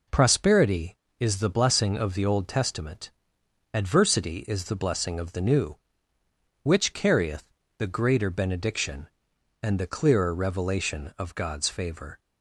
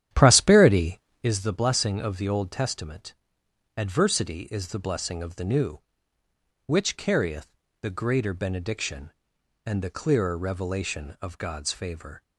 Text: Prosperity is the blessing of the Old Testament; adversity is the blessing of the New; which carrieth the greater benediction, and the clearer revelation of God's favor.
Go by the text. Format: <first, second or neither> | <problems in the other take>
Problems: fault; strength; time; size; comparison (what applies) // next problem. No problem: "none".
first | starts louder than the rest; strong; until 1.4 s; 10.5 dB // pauses between "carrieth" and "the"; slight; at 7.5 s; 0.26 s long; slight in the first